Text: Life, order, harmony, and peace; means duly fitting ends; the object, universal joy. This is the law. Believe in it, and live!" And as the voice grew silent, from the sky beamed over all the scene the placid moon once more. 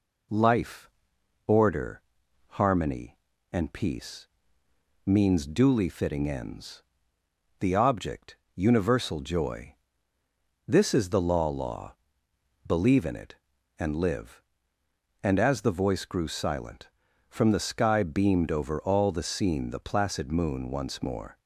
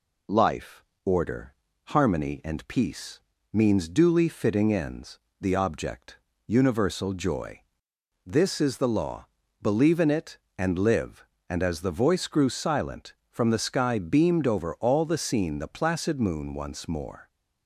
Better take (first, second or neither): second